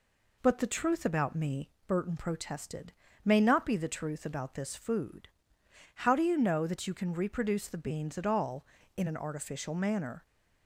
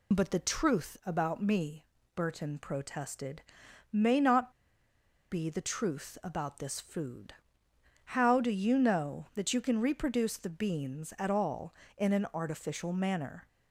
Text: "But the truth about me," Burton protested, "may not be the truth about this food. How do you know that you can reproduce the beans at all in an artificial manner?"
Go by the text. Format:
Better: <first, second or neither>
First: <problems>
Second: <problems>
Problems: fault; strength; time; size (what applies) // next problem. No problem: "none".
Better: first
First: none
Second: pauses between "not" and "be"; noticeable; at 4.5 s; 0.79 s long